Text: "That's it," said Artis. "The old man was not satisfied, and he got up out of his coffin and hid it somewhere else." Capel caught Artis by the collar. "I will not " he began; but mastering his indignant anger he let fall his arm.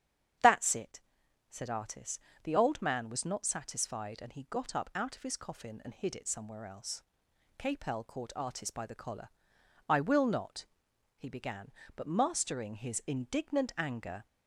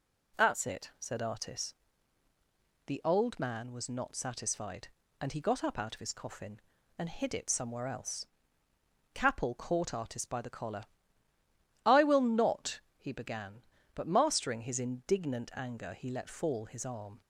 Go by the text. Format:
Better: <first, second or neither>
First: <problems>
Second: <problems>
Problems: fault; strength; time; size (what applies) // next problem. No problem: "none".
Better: second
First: starts louder than the rest; strong; until 1.9 s; 8.5 dB // stops before "he let fall his arm"; at 14.2 s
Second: none